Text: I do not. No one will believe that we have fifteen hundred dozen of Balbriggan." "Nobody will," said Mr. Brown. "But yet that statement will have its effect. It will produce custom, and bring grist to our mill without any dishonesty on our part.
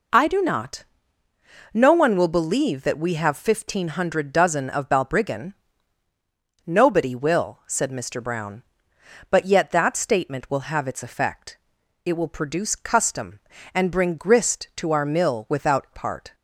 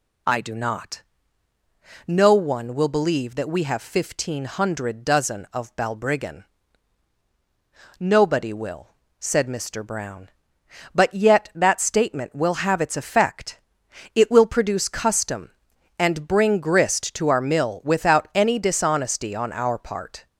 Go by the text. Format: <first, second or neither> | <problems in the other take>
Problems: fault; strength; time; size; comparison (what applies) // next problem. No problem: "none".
second | skips "any dishonesty on our"; at 15.8 s